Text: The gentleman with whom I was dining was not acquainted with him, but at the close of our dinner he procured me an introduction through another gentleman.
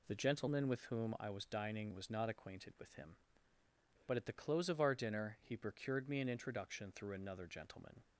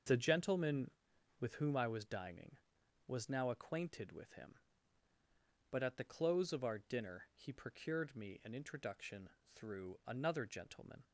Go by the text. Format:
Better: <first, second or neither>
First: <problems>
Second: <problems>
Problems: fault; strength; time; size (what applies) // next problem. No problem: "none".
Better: first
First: none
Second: starts louder than the rest; until 1.6 s; 6 dB // says "now" for "not"; at 3.2 s // pauses between "introduction" and "through"; slight; at 9.2 s; 0.26 s long